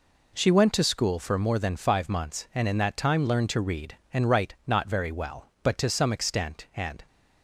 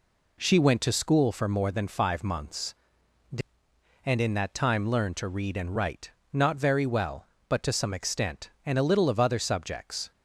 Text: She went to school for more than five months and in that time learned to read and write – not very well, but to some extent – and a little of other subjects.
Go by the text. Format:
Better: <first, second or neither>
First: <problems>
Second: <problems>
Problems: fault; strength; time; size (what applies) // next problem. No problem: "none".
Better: second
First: stops before "a little of other subjects"; at 7.0 s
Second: none